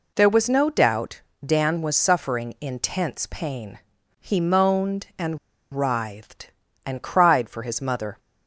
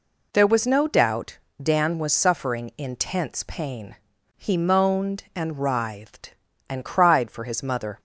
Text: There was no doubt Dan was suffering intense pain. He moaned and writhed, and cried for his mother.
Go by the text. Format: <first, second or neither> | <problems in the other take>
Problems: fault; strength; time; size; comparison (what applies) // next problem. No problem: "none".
second | pauses between "doubt" and "Dan"; slight; at 1.2 s; 0.20 s long; slight in the second // pauses between "and" and "writhed"; slight; at 5.3 s; 0.36 s long